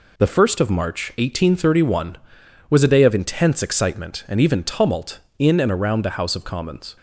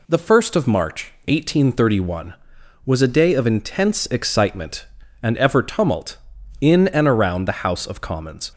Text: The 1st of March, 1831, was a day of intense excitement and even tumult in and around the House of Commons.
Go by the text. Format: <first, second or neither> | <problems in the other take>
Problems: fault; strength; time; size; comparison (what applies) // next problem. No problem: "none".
first | says "ever" for "even"; at 5.3 s